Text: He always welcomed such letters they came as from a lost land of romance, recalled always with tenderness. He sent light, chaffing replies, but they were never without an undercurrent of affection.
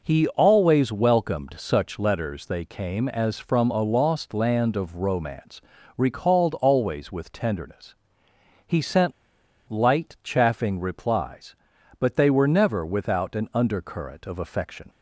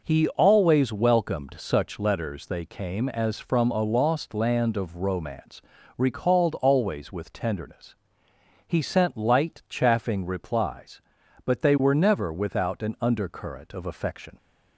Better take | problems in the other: second | pauses between "sent" and "light"; noticeable; at 9.1 s; 0.57 s long

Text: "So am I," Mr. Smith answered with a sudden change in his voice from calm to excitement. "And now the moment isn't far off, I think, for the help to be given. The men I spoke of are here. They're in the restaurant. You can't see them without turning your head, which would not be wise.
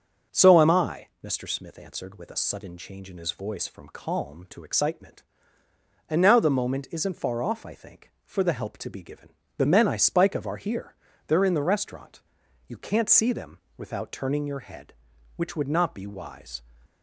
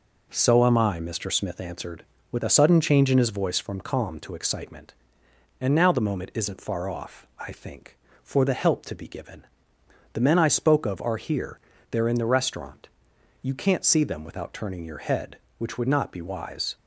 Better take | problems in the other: second | starts louder than the rest; until 1.4 s; 6.5 dB // says "spike" for "spoke"; at 9.9 s // pauses between "them" and "without"; slight; at 13.5 s; 0.18 s long

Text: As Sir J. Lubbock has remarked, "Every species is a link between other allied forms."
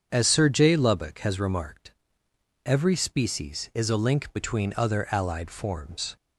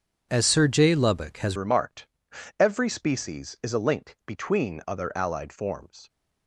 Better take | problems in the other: first | starts louder than the rest; strong; until 1.3 s; 7 dB; strong in the first // changes voice at "remarked"; from 1.5 s on; 4.5 s long

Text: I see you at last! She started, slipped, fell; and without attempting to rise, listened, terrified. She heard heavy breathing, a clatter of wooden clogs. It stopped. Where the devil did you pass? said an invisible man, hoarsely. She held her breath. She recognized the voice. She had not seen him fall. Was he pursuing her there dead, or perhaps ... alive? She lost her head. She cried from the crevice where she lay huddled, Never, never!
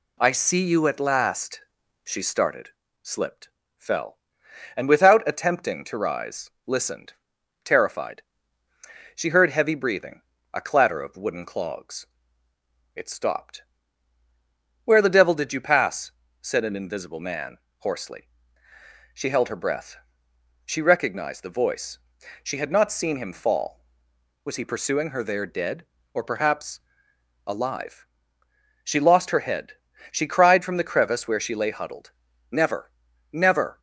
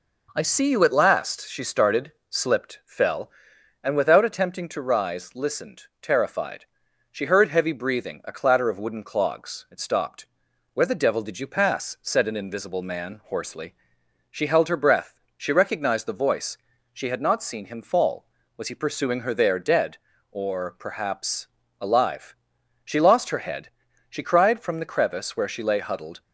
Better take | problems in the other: first | stops before "Never never"; at 26.2 s

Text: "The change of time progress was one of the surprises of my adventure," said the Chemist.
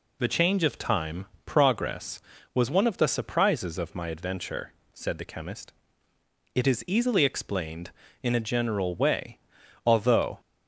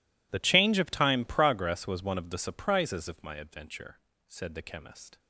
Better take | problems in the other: second | pauses between "time" and "progress"; slight; at 1.2 s; 0.20 s long // goes on to say "It is easily explained in a general way although"; strong; from 6.5 s on; 3.8 s long

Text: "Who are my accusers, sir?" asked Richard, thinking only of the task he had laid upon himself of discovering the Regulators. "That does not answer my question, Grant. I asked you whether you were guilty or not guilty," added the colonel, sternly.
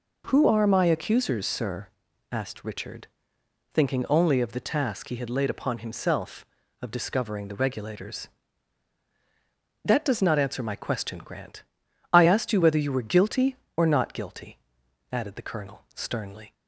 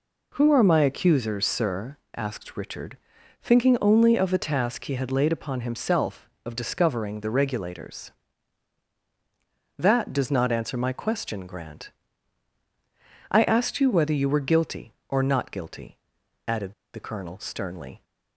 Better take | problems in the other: first | pauses between "added" and "the"; slight; at 16.7 s; 0.21 s long

